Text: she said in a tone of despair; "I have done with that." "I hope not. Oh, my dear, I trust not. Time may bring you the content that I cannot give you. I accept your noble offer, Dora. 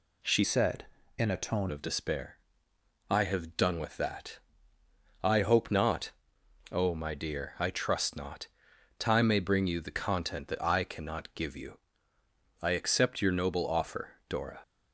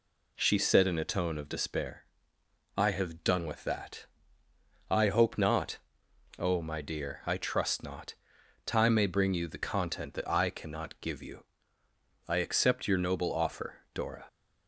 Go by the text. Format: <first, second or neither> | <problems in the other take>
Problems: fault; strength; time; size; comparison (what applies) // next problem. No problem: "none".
second | changes voice from "said" to "tone"; from 0.4 to 1.7 s; 1.3 s long